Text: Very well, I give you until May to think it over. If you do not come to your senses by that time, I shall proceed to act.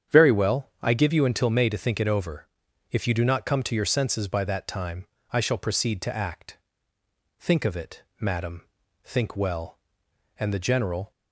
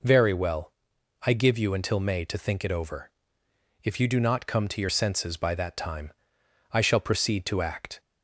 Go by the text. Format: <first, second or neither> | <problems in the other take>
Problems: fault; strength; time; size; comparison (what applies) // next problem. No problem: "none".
second | starts louder than the rest; strong; until 1.2 s; 8.5 dB // goes on to say "Think of it madam think well and the General"; strong; from 7.4 s on; 3.7 s long